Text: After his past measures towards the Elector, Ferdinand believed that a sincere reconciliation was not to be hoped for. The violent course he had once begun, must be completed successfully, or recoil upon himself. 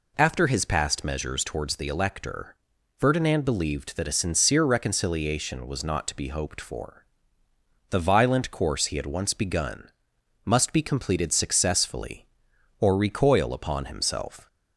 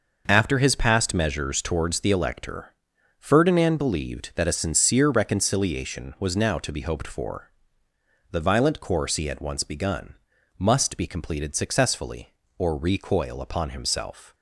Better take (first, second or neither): first